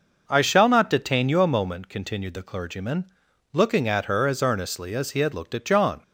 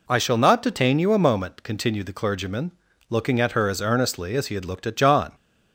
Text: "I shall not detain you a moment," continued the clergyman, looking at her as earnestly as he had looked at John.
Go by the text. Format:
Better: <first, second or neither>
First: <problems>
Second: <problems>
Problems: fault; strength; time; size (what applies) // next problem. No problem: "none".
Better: neither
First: none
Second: none